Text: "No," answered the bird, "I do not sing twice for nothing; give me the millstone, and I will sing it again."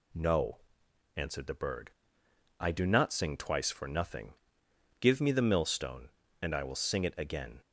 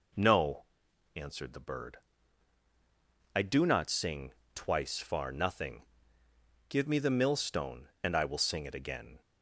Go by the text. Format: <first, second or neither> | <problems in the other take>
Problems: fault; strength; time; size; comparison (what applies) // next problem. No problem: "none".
first | pauses between "sing" and "twice"; slight; at 4.3 s; 0.18 s long // says "far" for "for"; at 4.9 s